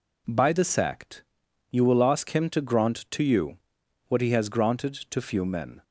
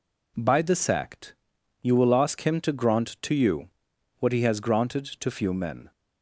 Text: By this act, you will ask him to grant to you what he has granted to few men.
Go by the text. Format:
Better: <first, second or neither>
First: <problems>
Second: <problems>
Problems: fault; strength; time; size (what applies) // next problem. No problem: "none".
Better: neither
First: pauses between "you" and "what"; noticeable; at 3.5 s; 0.50 s long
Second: pauses between "you" and "what"; noticeable; at 3.6 s; 0.50 s long